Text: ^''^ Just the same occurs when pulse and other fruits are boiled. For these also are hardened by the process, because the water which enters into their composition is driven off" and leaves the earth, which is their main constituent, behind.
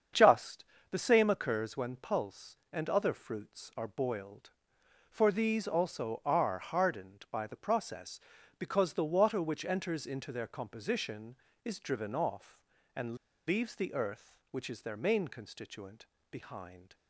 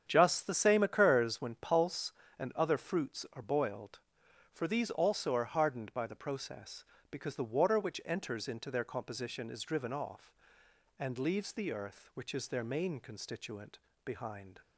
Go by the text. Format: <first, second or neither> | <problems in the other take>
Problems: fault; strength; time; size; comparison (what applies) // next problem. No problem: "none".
second | starts louder than the rest; strong; until 1.4 s; 7.5 dB; strong in the second // pauses between "Just" and "the"; slight; at 0.6 s; 0.28 s long // pauses between "and" and "leaves"; slight; at 13.1 s; 0.31 s long